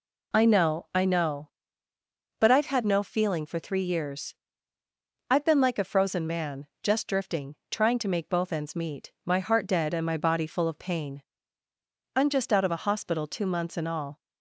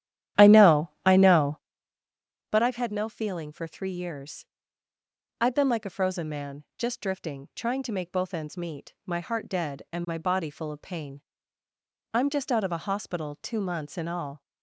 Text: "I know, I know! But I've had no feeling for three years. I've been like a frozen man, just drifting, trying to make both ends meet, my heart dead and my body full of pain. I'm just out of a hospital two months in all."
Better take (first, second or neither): first